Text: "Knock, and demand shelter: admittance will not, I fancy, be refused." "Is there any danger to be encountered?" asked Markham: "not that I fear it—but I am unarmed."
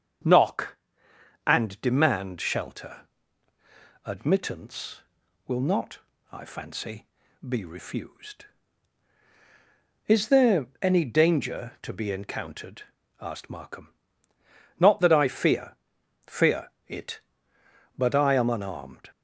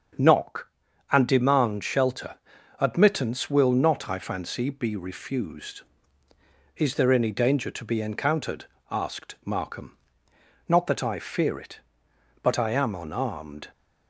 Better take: second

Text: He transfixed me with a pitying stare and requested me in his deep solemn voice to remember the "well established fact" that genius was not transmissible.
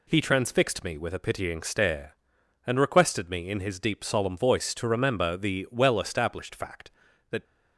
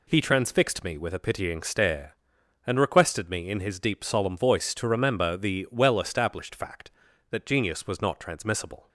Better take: second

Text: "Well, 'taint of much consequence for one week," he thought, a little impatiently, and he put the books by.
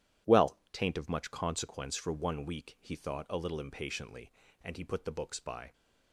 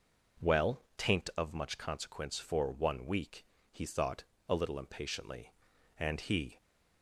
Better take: first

